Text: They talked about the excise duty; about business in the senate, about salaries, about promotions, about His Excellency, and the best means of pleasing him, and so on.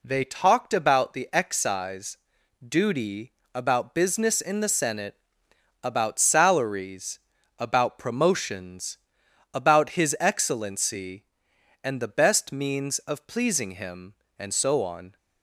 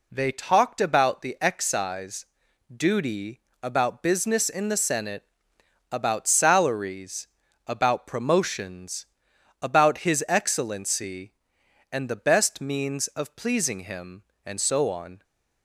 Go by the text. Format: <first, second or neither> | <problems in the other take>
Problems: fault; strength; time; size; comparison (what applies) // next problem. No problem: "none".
neither | pauses between "excise" and "duty"; noticeable; the same in both